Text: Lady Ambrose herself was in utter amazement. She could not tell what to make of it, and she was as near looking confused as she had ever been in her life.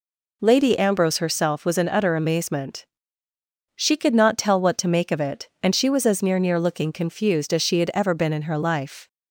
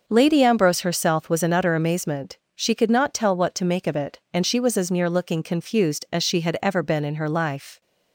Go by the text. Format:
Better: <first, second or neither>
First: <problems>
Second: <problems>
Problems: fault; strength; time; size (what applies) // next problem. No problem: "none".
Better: second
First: says "near" twice; at 6.3 s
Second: none